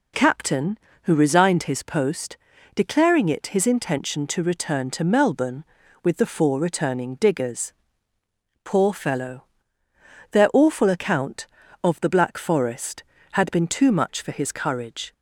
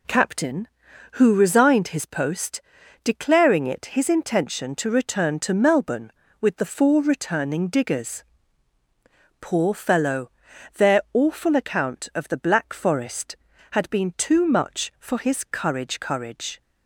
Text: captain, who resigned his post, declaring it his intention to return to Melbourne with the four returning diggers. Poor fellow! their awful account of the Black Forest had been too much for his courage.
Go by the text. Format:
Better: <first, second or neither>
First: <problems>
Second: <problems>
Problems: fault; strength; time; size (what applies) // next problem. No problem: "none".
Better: first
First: none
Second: says "courage" twice; at 15.9 s